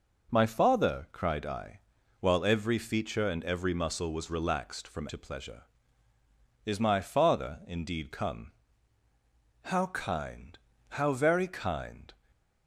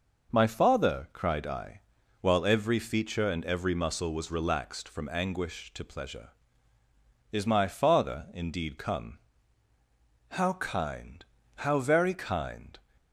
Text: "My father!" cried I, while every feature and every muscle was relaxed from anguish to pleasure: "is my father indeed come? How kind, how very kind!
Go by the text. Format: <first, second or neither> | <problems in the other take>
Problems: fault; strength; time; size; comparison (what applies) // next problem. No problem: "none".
second | skips "anguish"; at 5.0 s // stays silent after the last word; slight; from 12.1 s on; 0.5 s long